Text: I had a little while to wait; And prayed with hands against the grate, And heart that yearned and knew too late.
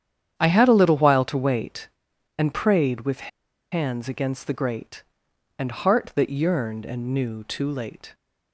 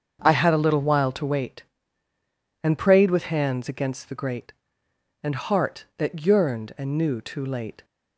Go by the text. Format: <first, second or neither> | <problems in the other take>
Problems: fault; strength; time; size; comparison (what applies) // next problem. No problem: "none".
second | starts louder than the rest; strong; until 1.3 s; 9 dB; also in the second // pauses between "with" and "hands"; at 3.2 s; 0.43 s long